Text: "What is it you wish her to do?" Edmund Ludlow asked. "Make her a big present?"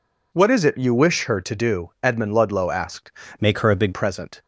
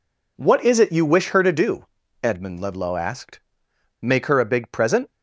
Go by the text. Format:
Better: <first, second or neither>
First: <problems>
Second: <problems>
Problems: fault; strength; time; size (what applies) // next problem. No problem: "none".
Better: second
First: changes voice from "Make" to "big"; from 3.4 to 3.9 s; 0.5 s long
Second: none